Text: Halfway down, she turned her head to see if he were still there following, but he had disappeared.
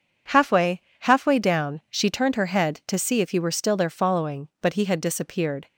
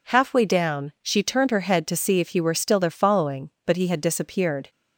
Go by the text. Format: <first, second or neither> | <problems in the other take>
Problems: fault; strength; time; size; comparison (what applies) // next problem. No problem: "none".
second | says "Halfway" twice; at 1.0 s